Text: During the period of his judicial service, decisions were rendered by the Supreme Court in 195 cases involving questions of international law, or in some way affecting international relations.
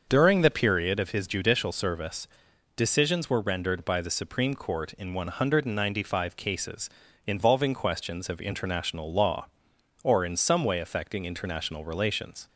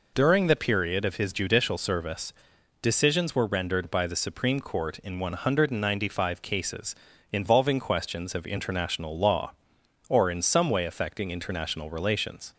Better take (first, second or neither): second